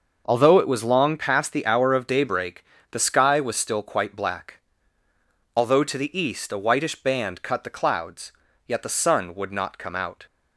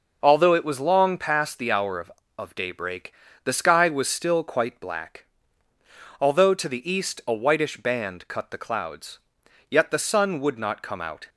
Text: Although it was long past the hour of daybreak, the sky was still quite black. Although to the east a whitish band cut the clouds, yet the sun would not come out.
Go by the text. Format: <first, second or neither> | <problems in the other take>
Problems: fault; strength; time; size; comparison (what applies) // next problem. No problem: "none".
first | says "of" twice; at 2.3 s